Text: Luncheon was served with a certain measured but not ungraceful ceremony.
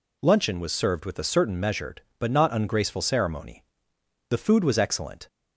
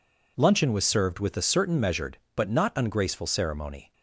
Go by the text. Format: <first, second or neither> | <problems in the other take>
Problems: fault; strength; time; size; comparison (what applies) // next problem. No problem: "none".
second | goes on to say "The food was excellent"; noticeable; from 4.2 s on; 0.98 s long